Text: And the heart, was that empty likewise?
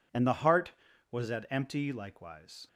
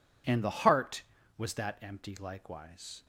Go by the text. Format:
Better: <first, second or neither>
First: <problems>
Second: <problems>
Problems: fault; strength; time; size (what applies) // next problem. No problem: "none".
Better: second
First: says "at" for "that"; at 1.2 s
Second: none